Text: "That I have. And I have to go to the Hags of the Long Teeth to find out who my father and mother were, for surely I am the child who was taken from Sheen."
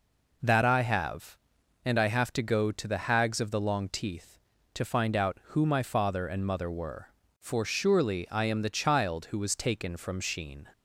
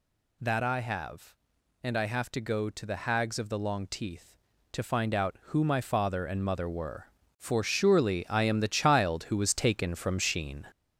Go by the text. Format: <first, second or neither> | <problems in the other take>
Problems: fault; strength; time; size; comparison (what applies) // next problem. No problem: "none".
first | gets louder; noticeable; throughout; 5 dB